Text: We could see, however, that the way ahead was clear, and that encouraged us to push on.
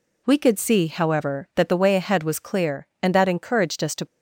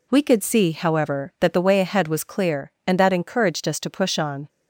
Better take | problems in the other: second | stops before "push on"; at 4.0 s

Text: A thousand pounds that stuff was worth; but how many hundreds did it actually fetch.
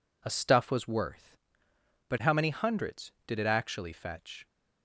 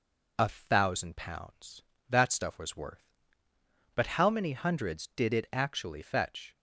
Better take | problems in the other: second | skips "thousand pounds that"; at 0.3 s

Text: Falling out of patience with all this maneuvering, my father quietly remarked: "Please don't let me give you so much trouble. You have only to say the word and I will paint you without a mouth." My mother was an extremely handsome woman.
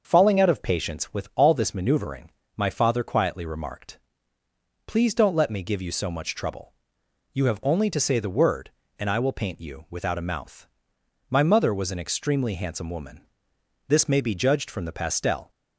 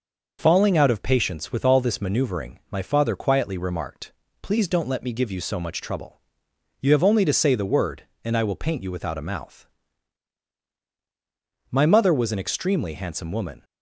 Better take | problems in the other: second | starts louder than the rest; until 1.1 s; 6 dB // goes on to say "This may be judged from the pastel"; from 13.8 s on; 1.6 s long

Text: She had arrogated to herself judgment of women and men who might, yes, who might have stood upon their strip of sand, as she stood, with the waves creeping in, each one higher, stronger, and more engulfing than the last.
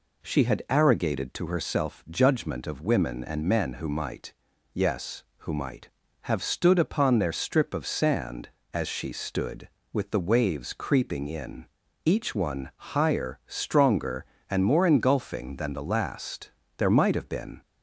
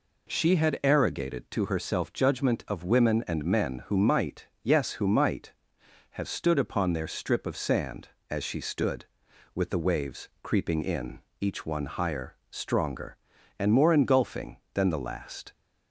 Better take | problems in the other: second | goes on to say "There might have been"; noticeable; from 16.7 s on; 0.84 s long

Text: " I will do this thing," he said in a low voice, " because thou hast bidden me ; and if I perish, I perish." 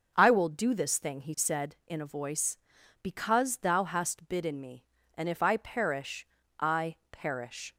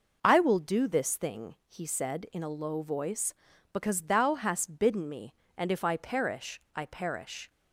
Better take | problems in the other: second | skips "low"; at 2.1 s

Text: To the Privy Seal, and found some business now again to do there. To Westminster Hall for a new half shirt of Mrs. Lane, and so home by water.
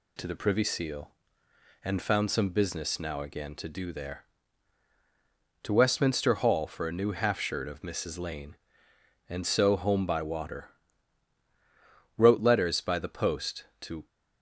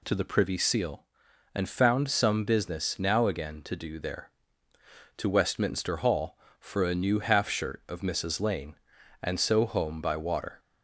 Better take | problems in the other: second | goes on to say "Wrote letters by the post to"; strong; from 12.1 s on; 1.9 s long

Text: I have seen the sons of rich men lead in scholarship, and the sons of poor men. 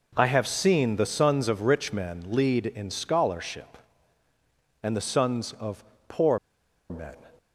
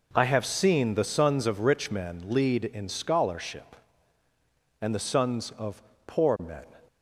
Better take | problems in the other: second | pauses between "of" and "poor"; slight; at 5.8 s; 0.24 s long; slight in the second // pauses between "poor" and "men"; noticeable; at 6.3 s; 0.52 s long

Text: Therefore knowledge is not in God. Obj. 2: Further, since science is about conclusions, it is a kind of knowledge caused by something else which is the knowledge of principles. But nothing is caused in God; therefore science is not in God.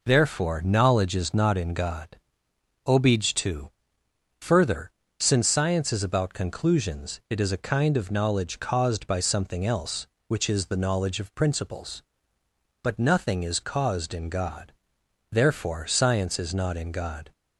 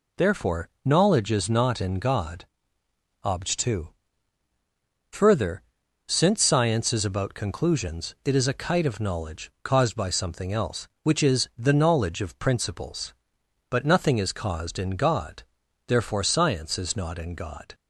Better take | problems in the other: first | pauses between "Therefore" and "knowledge"; slight; at 0.6 s; 0.16 s long // says "kite" for "kind"; at 8.5 s

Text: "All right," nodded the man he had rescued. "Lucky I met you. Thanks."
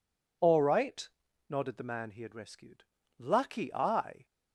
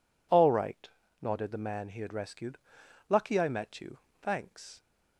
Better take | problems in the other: second | stops before "met you Thanks"; at 4.2 s

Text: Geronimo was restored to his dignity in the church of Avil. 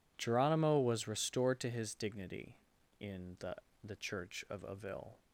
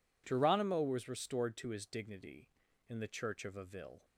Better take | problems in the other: second | says "the" twice; at 3.8 s

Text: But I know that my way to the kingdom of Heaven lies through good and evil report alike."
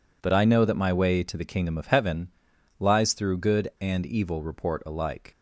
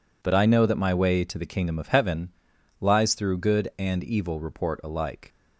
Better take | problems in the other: neither | pauses between "Heaven" and "lies"; noticeable; the same in both

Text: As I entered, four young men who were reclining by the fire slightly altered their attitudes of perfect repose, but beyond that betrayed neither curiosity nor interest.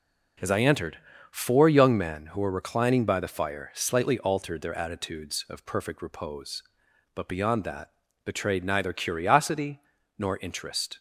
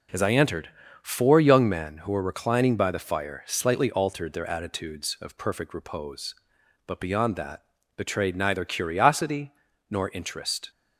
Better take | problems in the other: neither | pauses between "that" and "betrayed"; slight; the same in both // pauses between "curiosity" and "nor"; the same in both

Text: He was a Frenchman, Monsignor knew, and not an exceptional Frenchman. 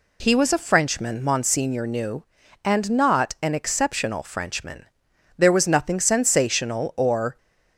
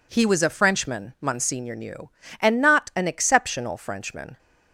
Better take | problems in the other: second | goes on to say "There was nothing sensational or"; strong; from 5.3 s on; 2.0 s long

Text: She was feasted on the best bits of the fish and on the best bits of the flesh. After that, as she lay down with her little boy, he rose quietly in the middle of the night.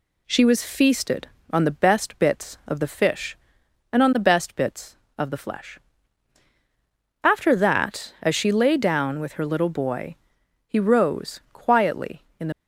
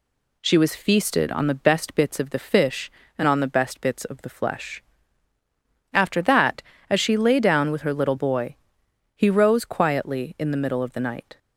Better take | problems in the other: second | stops before "middle of the night"; at 12.5 s

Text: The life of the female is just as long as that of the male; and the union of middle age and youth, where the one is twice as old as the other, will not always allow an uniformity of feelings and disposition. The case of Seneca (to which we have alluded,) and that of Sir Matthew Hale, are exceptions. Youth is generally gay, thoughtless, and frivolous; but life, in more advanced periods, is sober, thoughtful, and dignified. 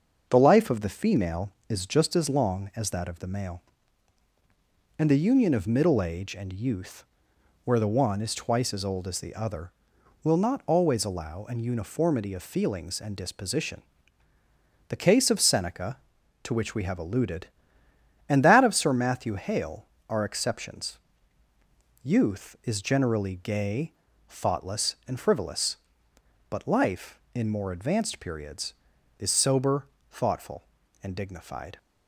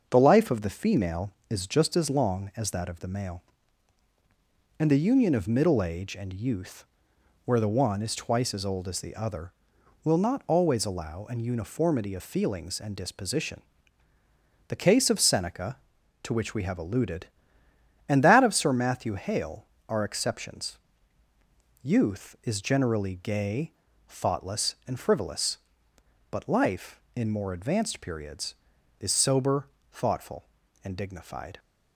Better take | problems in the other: neither | starts louder than the rest; the same in both

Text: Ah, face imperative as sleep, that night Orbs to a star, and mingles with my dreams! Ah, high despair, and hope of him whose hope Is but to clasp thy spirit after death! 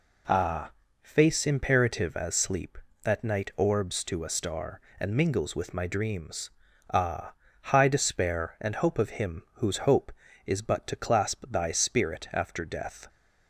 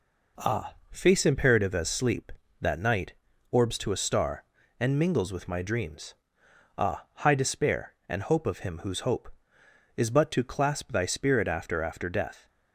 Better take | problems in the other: first | pauses between "night" and "Orbs"; at 3.1 s; 0.38 s long // says "after" twice; at 11.8 s

